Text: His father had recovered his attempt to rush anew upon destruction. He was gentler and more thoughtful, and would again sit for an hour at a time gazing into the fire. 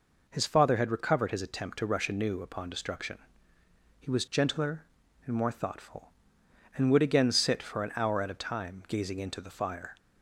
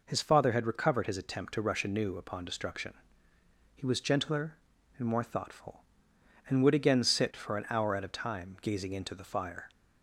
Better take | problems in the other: neither | none

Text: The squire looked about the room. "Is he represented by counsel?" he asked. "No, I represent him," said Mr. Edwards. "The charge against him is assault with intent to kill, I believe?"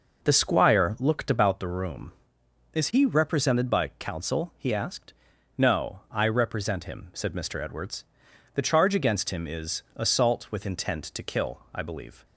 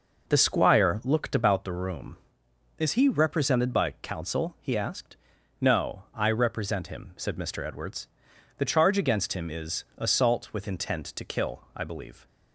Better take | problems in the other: neither | none

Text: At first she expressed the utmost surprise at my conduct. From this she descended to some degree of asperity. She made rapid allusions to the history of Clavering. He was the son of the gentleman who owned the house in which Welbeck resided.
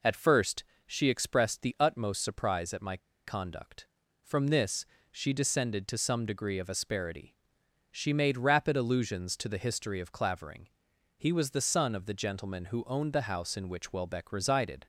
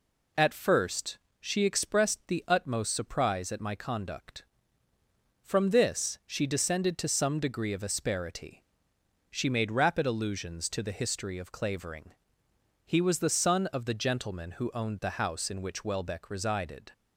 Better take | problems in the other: second | pauses between "first" and "she"; slight; at 0.6 s; 0.22 s long; slight in the second // pauses between "my" and "conduct"; slight; at 2.9 s; 0.29 s long // pauses between "this" and "she"; slight; at 4.8 s; 0.26 s long

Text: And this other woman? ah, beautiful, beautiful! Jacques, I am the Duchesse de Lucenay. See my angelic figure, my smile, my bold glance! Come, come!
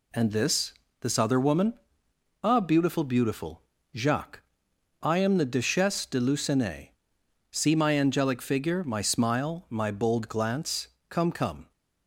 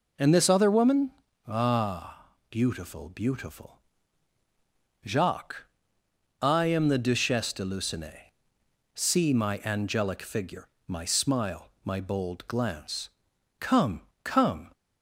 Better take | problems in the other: second | says "this" twice; at 0.9 s

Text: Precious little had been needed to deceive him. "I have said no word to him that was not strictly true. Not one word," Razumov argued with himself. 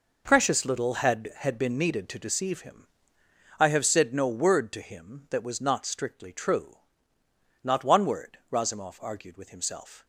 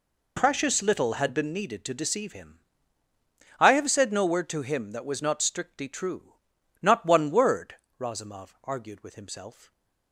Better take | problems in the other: second | says "had" twice; at 1.3 s

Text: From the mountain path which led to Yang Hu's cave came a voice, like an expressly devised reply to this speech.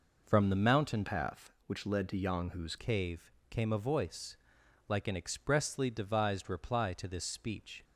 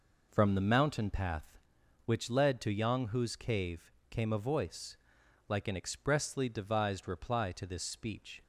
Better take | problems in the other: second | changes voice from "path" to "Hu's"; from 1.0 to 2.7 s; 1.7 s long // pauses between "cave" and "came"; slight; at 3.2 s; 0.20 s long; slight in the second

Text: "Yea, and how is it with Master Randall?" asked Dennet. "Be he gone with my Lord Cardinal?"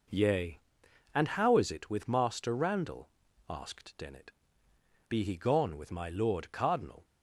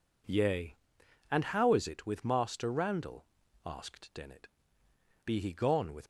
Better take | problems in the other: first | stops before "my Lord Cardinal"; at 6.0 s

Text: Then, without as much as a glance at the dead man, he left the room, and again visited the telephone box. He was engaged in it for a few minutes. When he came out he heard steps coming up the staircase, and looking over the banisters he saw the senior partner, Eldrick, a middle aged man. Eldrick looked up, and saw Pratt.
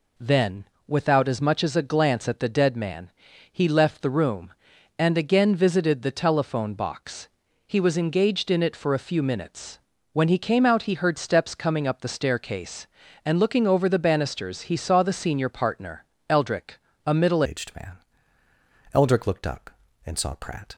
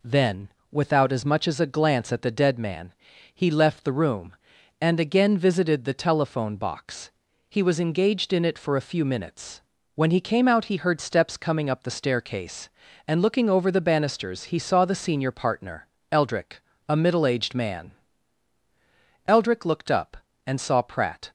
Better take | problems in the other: second | changes voice at "aged"; from 17.4 s on; 3.3 s long

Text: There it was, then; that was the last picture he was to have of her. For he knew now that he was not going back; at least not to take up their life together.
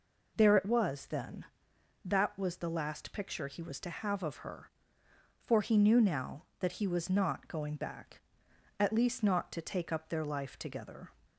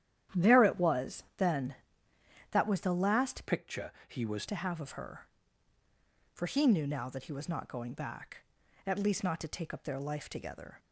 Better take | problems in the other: first | starts louder than the rest; strong; until 1.4 s; 11 dB // changes voice from "picture" to "was"; from 3.4 to 4.4 s; 1.0 s long // pauses between "picture" and "he"; slight; at 3.9 s; 0.16 s long

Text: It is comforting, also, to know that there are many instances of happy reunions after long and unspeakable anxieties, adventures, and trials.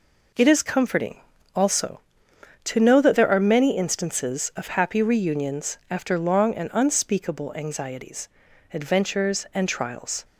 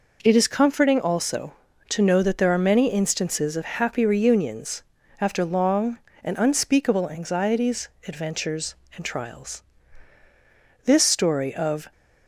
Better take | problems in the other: first | pauses between "reunions" and "after"; slight; at 4.8 s; 0.36 s long // goes on to say "This story of"; noticeable; from 10.8 s on; 1.0 s long

